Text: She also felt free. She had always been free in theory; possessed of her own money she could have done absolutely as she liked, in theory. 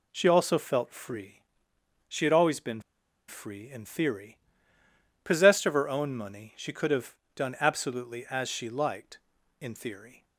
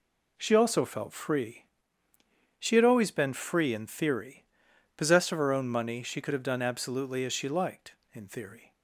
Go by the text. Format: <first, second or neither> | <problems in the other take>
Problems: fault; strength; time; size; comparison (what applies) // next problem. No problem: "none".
second | pauses between "been" and "free"; noticeable; at 2.7 s; 0.48 s long // pauses between "have" and "done"; slight; at 7.1 s; 0.22 s long